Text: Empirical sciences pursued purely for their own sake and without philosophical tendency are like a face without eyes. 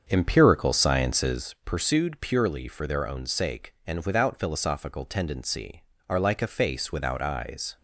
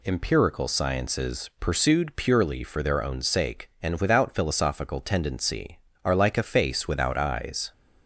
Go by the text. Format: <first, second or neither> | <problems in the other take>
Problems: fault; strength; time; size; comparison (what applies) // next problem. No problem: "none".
second | starts louder than the rest; until 1.5 s; 7 dB